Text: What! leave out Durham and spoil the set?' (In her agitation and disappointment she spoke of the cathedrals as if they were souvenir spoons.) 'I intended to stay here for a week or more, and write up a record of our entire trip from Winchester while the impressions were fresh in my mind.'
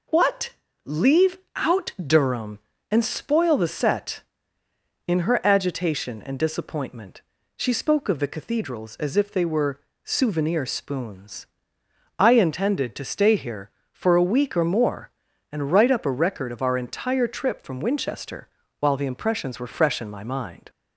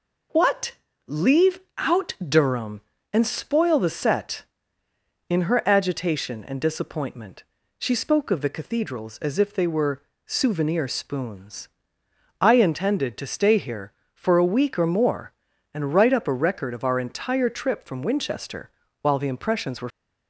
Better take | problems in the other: first | pauses between "leave" and "out"; slight; at 1.5 s; 0.18 s long; slight in the first // pauses between "disappointment" and "she"; at 7.4 s; 0.38 s long; also in the first // pauses between "were" and "souvenir"; slight; at 10.0 s; 0.24 s long; slight in the first // pauses between "Winchester" and "while"; slight; at 18.6 s; 0.32 s long; slight in the first // stops before "fresh in my mind"; at 19.8 s

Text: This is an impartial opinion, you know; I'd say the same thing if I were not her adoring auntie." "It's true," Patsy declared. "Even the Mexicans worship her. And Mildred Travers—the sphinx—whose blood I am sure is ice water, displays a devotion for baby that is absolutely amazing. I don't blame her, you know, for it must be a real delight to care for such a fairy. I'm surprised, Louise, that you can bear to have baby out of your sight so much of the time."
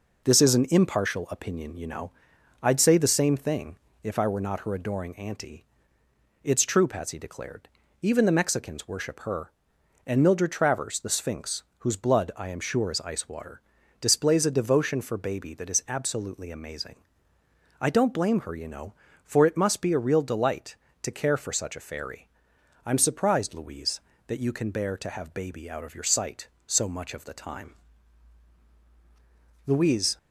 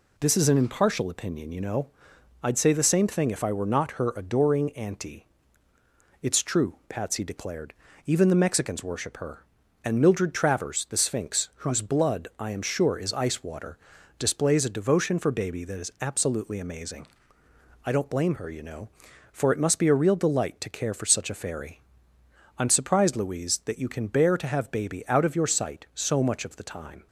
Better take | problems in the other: second | pauses between "thing" and "if"; slight; at 3.7 s; 0.26 s long // goes on to say "Louise"; from 29.6 s on; 0.50 s long

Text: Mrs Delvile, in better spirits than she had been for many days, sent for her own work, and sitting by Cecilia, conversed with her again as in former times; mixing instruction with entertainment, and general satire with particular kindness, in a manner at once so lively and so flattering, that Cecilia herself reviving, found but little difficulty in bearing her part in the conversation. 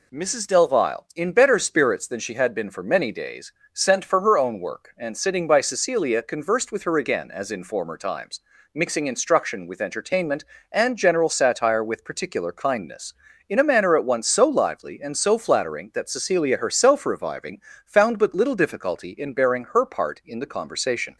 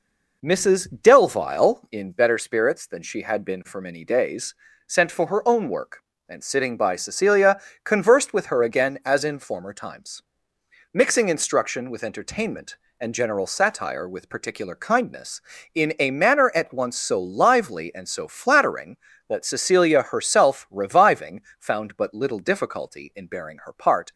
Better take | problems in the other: first | stops before "in the conversation"; at 24.1 s

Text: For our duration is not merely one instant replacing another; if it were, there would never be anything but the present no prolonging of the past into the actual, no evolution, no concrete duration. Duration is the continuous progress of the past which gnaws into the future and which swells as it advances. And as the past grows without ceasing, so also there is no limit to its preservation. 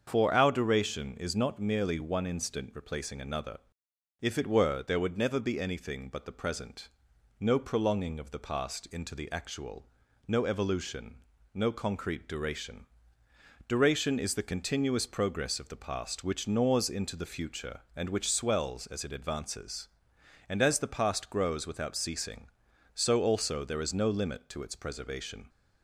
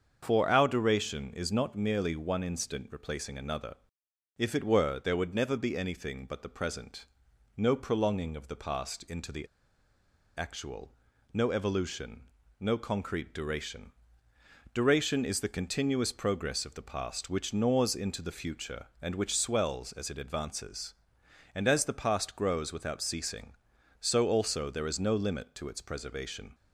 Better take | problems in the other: first | starts louder than the rest; until 1.2 s; 7 dB; also in the first // pauses between "present" and "no"; noticeable; at 7.0 s; 0.54 s long; noticeable in the first // pauses between "the" and "actual"; noticeable; at 9.4 s; 0.93 s long

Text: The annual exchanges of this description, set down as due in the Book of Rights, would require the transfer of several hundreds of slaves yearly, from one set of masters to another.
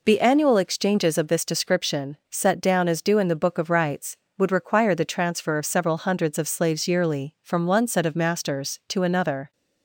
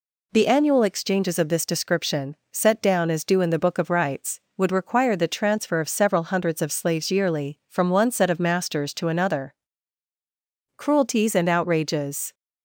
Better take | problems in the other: first | goes on to say "Cruelties and outrages"; from 10.7 s on; 1.5 s long

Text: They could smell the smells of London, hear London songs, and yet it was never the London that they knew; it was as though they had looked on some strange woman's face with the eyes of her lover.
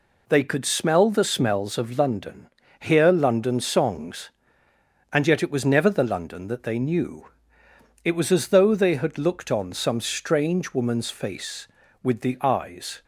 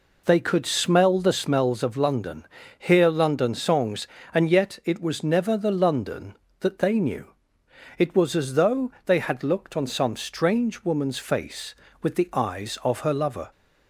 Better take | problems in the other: second | stops before "of her lover"; at 13.0 s

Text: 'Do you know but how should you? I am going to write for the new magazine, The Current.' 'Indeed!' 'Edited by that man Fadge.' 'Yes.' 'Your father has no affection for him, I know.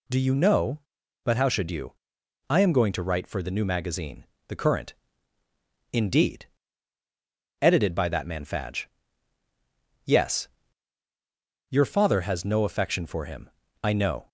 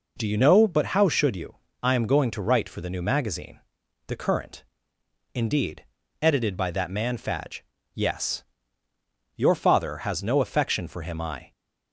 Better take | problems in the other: first | stops before "know"; at 11.5 s

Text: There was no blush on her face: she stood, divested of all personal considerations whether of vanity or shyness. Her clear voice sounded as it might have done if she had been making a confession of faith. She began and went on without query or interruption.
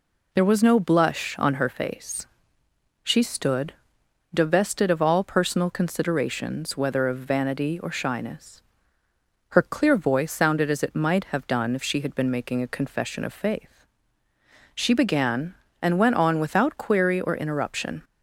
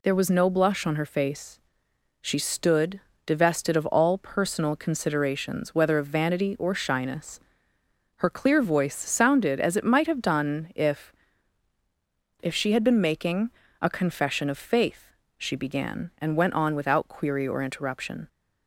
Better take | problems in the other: first | says "if" twice; at 12.4 s // pauses between "making" and "a"; slight; at 13.4 s; 0.32 s long

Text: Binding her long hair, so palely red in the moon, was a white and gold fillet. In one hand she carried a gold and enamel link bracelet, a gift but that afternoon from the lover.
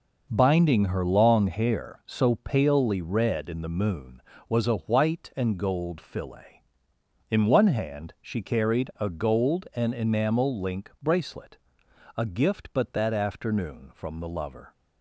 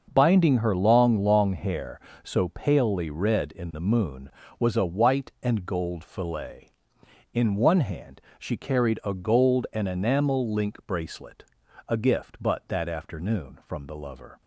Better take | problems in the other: first | starts louder than the rest; until 1.1 s; 6.5 dB // says "long" twice; at 1.2 s // pauses between "hand" and "she"; slight; at 8.1 s; 0.18 s long

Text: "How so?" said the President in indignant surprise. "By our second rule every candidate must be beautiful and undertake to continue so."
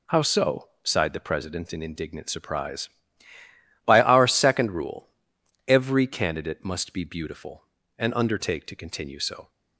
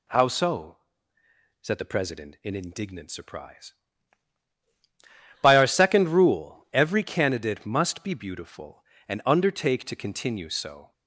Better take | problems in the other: second | says "sighed" for "said"; at 0.8 s // pauses between "rule" and "every"; noticeable; at 5.0 s; 0.58 s long

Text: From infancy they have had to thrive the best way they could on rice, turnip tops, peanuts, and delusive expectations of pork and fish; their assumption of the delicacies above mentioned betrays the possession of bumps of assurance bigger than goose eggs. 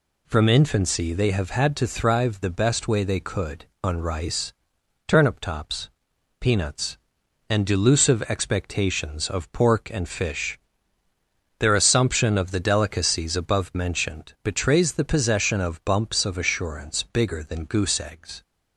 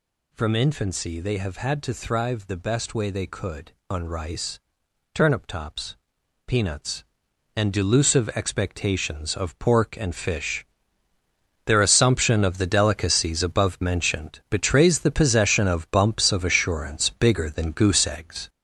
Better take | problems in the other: first | gets louder; noticeable; throughout; 4.5 dB

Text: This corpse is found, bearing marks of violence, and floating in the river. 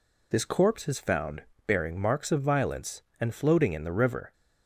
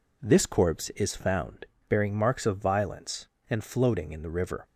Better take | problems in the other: neither | none

